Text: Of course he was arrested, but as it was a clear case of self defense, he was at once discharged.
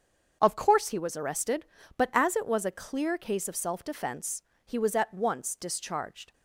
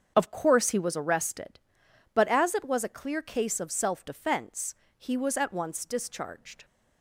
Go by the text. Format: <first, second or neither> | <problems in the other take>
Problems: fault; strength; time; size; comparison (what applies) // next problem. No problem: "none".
neither | starts louder than the rest; the same in both